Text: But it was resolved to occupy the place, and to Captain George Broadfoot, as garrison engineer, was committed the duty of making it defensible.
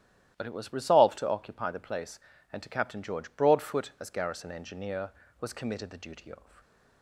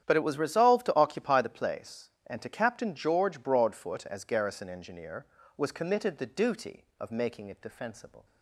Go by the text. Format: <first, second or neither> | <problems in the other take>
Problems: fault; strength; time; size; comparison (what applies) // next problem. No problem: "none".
second | starts louder than the rest; strong; until 1.3 s; 12.5 dB; strong in the second // stops before "making it defensible"; at 6.6 s